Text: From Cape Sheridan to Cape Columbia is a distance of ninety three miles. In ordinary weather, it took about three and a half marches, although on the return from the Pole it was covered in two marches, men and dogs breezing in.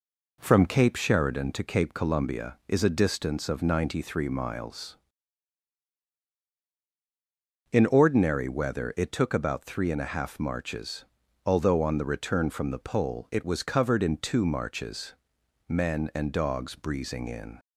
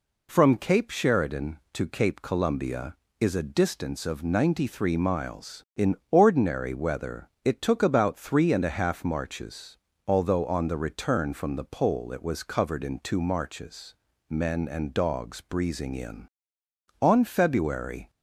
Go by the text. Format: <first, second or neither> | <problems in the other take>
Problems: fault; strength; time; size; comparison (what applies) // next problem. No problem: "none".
first | pauses between "In" and "ordinary"; slight; at 5.9 s; 0.16 s long // goes on to say "On February"; noticeable; from 17.0 s on; 1.0 s long